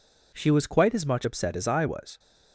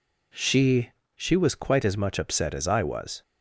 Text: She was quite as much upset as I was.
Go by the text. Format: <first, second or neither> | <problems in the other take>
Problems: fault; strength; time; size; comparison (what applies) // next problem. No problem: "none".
first | says "She" twice; at 1.1 s